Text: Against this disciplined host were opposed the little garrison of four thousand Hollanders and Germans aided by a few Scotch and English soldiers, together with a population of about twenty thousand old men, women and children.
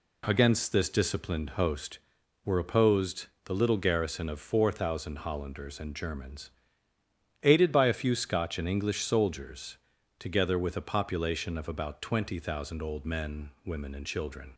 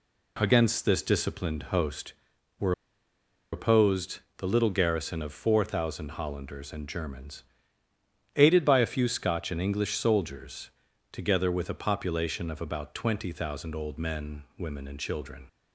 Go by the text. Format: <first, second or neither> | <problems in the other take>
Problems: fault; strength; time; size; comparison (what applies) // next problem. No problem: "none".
first | pauses between "were" and "opposed"; noticeable; at 2.7 s; 0.81 s long // pauses between "opposed" and "the"; slight; at 4.1 s; 0.16 s long; slight in the first // pauses between "Germans" and "aided"; noticeable; at 7.4 s; 0.94 s long; noticeable in the first